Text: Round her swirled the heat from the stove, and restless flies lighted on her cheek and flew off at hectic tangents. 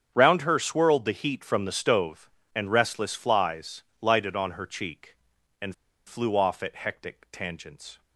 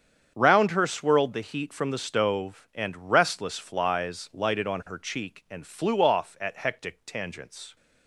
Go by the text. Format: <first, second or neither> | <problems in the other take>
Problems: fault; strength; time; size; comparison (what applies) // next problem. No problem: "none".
second | starts louder than the rest; strong; until 1.1 s; 8 dB; strong in the second // pauses between "flies" and "lighted"; slight; at 3.8 s; 0.18 s long // pauses between "and" and "flew"; slight; at 5.7 s; 0.31 s long